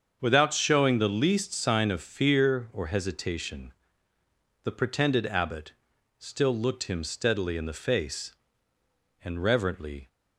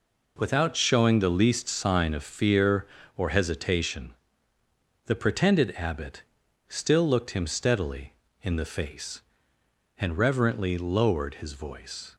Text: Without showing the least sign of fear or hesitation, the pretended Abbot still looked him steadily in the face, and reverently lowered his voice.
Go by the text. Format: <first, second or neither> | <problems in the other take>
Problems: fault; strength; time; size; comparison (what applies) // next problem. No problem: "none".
second | starts louder than the rest; until 1.2 s; 7 dB // pauses between "Abbot" and "still"; noticeable; at 5.7 s; 0.46 s long; noticeable in the second // stops before "lowered his voice"; at 10.0 s